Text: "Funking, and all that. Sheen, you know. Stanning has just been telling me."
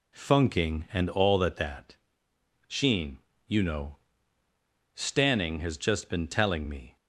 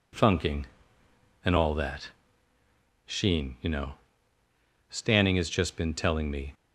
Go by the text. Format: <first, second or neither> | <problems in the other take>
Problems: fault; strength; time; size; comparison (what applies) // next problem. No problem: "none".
second | says "that" twice; at 1.5 s